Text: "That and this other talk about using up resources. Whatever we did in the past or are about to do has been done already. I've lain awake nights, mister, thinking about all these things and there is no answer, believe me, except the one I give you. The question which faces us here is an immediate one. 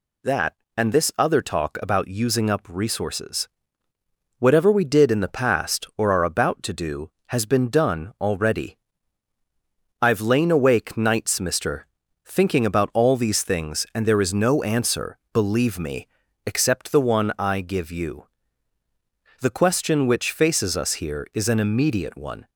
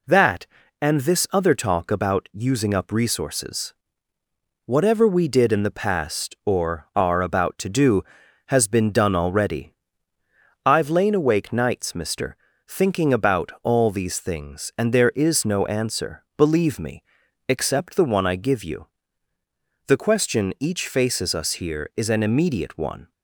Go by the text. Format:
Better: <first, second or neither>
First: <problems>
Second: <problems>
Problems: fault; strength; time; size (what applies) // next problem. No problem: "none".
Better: first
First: none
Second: says "each" for "which"; at 20.5 s